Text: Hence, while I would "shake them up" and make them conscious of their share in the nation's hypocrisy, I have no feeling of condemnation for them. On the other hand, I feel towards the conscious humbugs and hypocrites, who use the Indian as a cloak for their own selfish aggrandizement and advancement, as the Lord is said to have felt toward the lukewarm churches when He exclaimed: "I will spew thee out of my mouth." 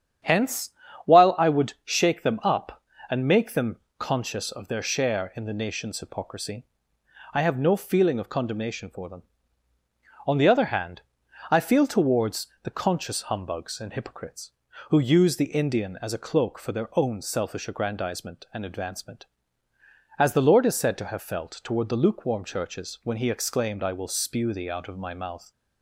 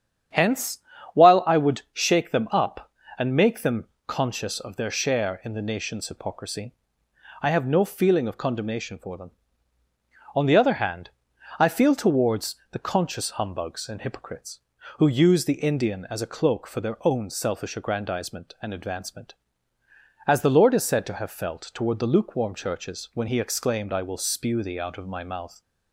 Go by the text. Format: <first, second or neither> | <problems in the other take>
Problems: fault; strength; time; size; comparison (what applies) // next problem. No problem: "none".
neither | starts louder than the rest; strong; the same in both // pauses between "them" and "conscious"; slight; the same in both // pauses between "towards" and "the"; slight; the same in both